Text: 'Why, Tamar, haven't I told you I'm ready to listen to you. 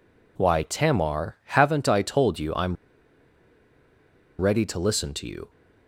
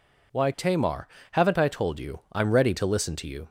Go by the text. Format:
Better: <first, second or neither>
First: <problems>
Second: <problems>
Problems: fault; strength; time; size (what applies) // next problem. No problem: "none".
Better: second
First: pauses between "I'm" and "ready"; strong; at 2.7 s; 1.6 s long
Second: none